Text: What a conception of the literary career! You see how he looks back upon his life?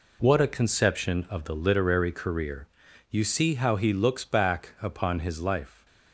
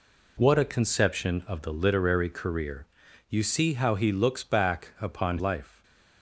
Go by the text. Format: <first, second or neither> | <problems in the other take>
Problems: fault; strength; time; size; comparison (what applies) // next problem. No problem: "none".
first | skips "his"; at 5.3 s // stays silent after the last word; slight; from 5.6 s on; 0.6 s long